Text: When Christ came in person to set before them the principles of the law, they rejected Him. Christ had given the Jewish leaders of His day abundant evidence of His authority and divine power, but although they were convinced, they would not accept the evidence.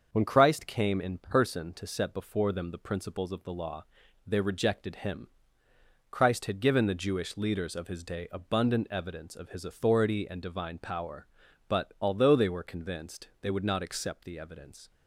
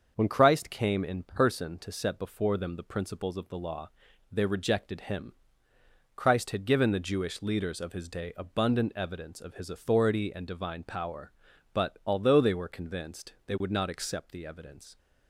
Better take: neither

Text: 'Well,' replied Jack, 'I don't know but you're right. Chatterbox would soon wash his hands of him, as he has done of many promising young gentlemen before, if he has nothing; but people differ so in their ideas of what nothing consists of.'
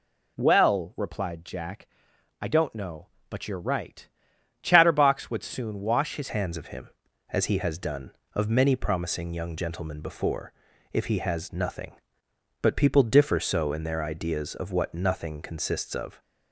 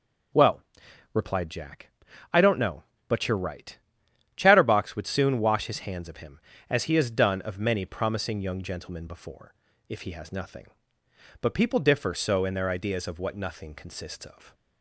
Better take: second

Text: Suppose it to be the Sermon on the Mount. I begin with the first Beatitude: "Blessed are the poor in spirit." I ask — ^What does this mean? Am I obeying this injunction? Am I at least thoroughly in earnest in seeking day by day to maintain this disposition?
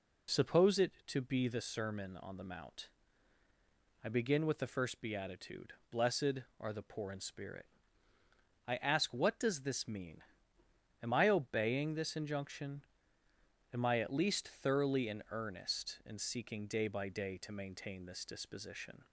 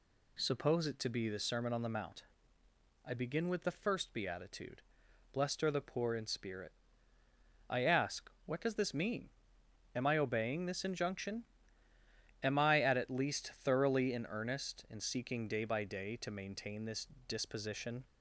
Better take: first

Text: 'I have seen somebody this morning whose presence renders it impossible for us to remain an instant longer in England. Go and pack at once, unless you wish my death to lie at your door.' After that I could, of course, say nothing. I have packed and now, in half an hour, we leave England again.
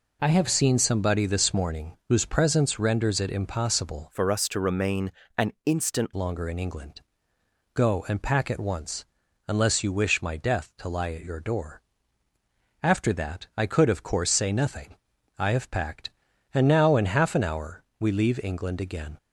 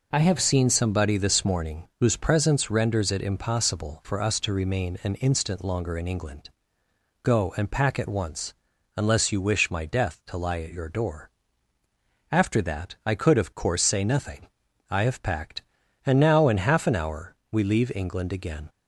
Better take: second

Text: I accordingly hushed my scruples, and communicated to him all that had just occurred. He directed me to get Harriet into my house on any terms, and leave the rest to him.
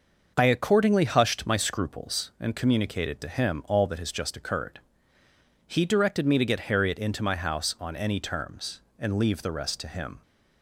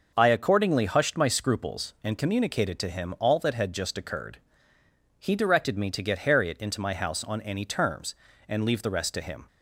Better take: second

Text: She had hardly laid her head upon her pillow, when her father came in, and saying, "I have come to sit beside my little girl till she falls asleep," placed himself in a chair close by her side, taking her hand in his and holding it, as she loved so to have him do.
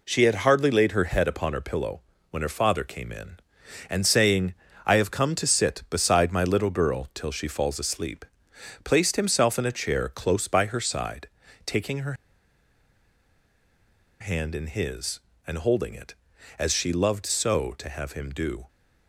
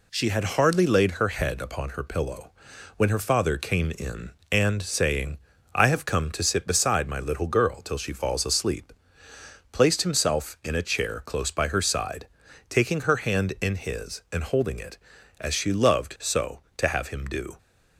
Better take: second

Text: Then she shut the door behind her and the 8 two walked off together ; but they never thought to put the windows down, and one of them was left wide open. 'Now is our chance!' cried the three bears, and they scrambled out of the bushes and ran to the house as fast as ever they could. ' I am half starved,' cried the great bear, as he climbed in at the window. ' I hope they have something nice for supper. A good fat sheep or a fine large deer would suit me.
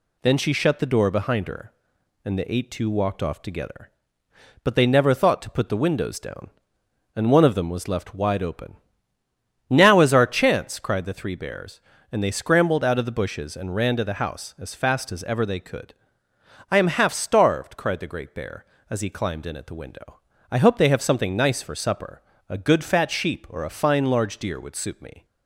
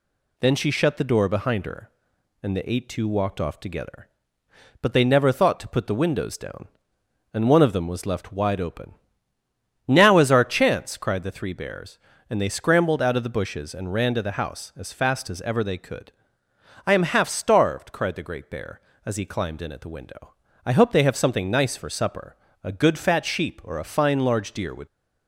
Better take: first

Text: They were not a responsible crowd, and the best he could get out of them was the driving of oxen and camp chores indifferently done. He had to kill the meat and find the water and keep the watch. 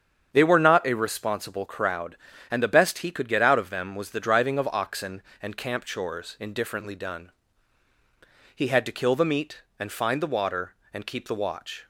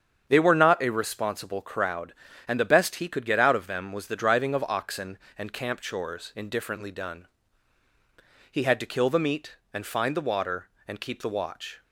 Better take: neither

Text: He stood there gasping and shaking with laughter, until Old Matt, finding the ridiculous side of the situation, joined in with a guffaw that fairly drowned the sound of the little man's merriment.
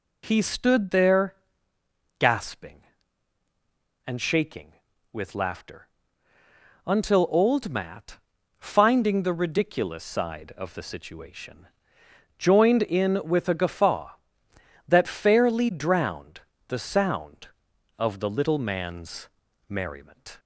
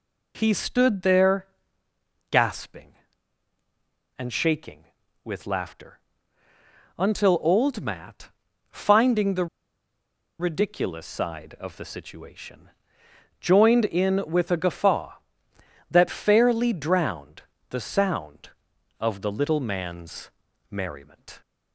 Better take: first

